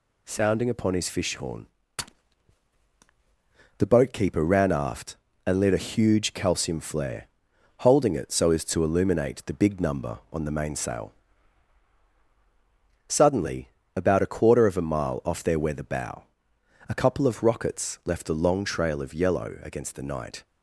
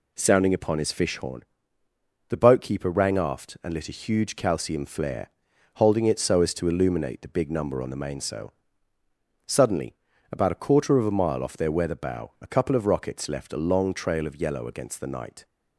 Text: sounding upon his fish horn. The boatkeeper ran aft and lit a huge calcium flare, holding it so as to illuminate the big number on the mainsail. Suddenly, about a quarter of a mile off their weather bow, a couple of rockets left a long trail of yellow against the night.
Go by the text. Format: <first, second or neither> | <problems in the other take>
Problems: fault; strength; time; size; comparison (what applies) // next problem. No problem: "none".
first | says "rang" for "ran"; at 2.9 s